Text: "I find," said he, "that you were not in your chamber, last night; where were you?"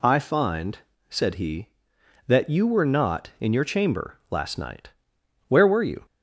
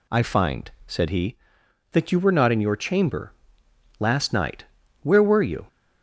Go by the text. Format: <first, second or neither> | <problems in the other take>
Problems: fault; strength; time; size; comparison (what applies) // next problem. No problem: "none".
neither | none